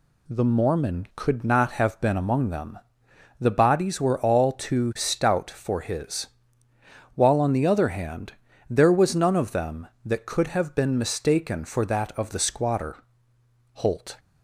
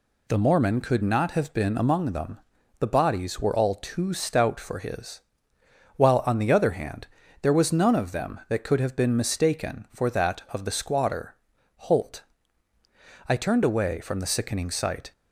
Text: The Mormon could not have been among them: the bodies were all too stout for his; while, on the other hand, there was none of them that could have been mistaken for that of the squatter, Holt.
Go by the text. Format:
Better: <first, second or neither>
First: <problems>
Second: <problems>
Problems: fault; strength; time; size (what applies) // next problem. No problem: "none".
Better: first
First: none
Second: goes on to say "I turned away from the sickening sight"; strong; from 13.2 s on; 1.8 s long